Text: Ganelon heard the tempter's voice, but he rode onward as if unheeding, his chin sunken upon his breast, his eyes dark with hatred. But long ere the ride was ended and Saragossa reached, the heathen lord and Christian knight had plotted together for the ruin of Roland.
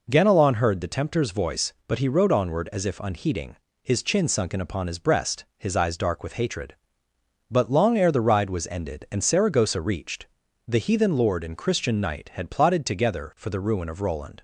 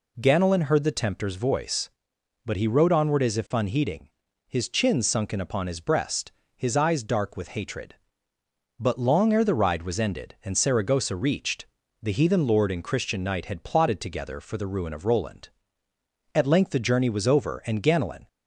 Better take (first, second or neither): first